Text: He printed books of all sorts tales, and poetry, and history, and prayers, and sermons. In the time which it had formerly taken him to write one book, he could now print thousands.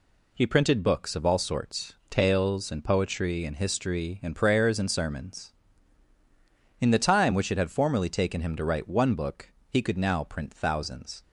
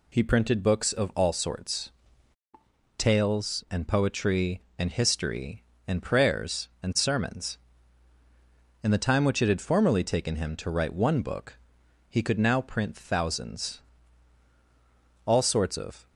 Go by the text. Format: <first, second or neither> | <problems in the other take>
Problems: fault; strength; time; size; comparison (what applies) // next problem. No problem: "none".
first | pauses between "sorts" and "tales"; at 1.9 s; 1.0 s long // goes on to say "All sorts of"; noticeable; from 15.2 s on; 0.82 s long